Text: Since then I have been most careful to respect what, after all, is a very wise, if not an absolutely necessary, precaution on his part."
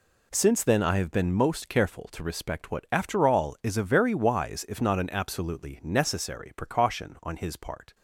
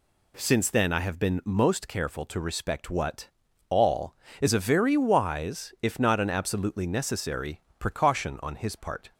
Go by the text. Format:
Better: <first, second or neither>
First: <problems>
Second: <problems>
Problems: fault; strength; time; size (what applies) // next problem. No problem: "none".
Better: first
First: none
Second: skips "after"; at 3.4 s